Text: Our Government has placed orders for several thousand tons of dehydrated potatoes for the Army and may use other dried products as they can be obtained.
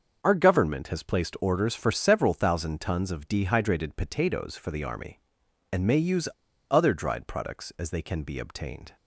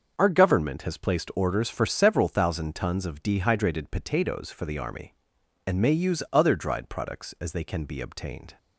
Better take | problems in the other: second | starts louder than the rest; until 1.2 s; 6.5 dB; also in the second // pauses between "use" and "other"; at 6.2 s; 0.44 s long

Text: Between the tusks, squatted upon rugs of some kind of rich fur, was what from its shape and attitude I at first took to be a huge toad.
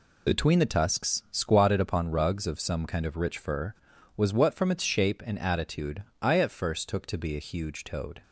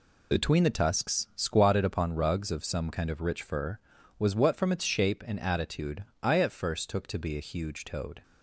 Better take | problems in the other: neither | pauses between "attitude" and "I"; slight; the same in both

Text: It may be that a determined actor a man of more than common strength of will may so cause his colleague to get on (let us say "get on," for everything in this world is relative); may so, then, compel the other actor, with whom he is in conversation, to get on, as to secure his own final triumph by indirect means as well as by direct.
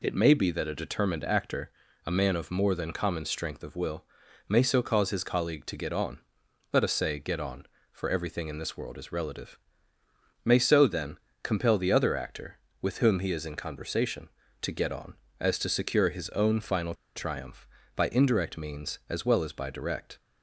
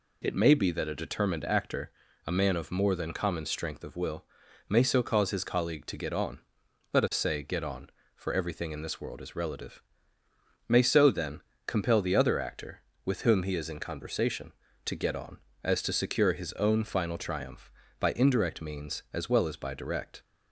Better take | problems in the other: second | pauses between "actor" and "a"; slight; at 1.7 s; 0.34 s long; slight in the second // pauses between "will" and "may"; noticeable; at 4.0 s; 0.46 s long; noticeable in the second // pauses between "final" and "triumph"; slight; at 16.9 s; 0.21 s long

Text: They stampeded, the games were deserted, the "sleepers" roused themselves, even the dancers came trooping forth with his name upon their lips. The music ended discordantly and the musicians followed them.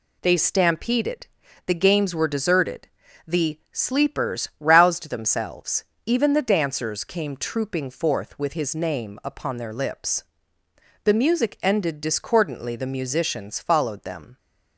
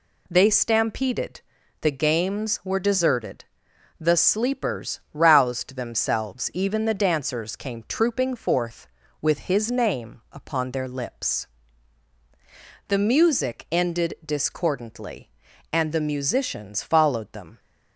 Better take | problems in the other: second | skips "and"; at 12.7 s

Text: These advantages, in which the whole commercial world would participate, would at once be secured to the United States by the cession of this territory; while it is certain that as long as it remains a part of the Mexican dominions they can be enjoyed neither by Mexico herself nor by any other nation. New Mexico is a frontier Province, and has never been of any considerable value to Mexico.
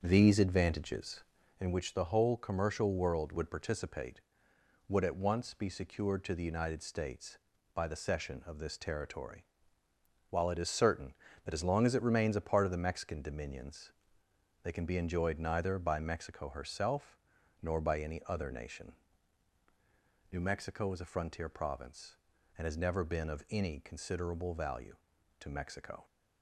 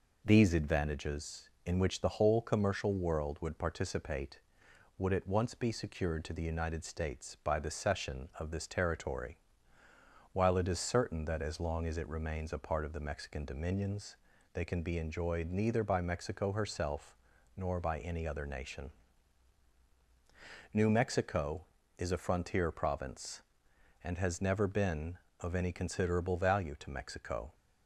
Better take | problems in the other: second | starts louder than the rest; until 1.6 s; 6.5 dB // pauses between "dominions" and "they"; noticeable; at 13.9 s; 0.72 s long; slight in the second // pauses between "herself" and "nor"; at 17.1 s; 0.44 s long; also in the second

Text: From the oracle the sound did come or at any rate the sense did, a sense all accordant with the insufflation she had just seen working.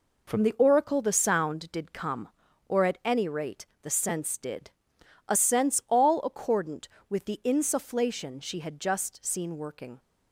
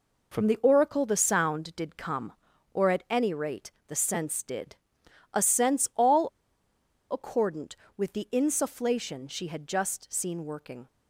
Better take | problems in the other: first | pauses between "rate" and "the"; slight; at 3.7 s; 0.18 s long; slight in the first // pauses between "all" and "accordant"; noticeable; at 6.2 s; 0.84 s long

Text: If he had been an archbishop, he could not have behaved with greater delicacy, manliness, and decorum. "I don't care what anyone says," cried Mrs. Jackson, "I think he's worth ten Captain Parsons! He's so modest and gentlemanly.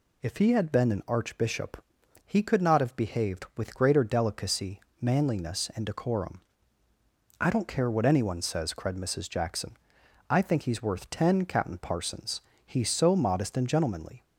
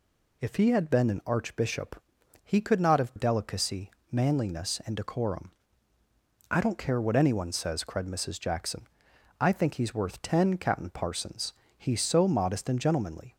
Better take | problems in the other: first | skips "behaved with greater"; at 3.1 s

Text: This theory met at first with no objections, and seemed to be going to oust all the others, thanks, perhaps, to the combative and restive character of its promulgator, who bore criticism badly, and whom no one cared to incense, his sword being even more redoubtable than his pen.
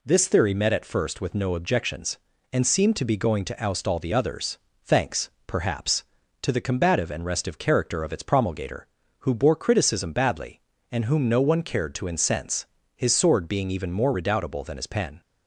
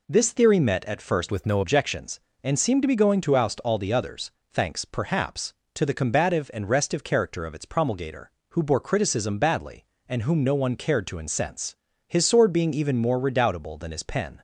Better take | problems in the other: first | changes voice from "with" to "no"; from 1.3 to 1.6 s; 0.3 s long

